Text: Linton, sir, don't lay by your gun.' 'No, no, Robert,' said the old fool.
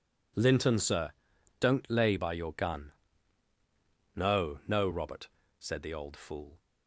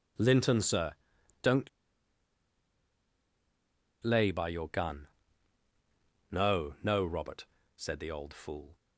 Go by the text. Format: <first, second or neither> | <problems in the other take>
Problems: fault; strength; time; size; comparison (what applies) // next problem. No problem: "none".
first | pauses between "don't" and "lay"; strong; at 1.6 s; 2.3 s long